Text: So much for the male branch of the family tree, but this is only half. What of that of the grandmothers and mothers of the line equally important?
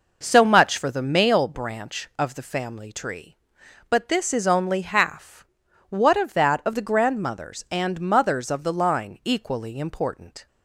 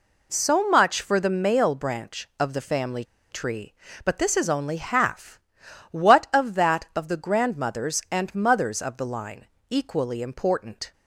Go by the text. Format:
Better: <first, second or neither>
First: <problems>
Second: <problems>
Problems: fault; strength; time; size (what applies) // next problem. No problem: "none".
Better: first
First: none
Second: pauses between "family" and "tree"; slight; at 3.0 s; 0.28 s long // pauses between "line" and "equally"; slight; at 9.4 s; 0.22 s long